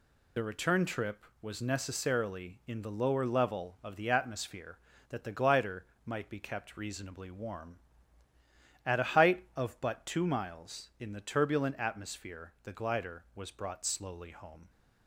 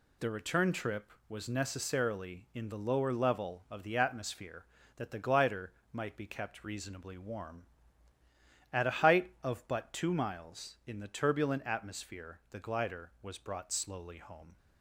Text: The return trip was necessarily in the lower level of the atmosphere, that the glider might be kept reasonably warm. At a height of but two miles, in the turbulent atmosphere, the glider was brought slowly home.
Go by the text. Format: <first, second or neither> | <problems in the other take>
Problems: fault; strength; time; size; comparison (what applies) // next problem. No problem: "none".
second | loses the start of "The"; at 0.3 s; 30 ms // pauses between "glider" and "might"; slight; at 5.8 s; 0.22 s long; slight in the second